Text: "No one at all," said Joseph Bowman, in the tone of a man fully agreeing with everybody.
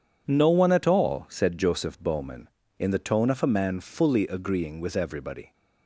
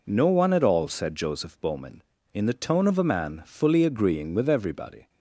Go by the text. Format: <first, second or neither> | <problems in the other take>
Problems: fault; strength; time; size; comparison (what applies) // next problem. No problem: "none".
neither | none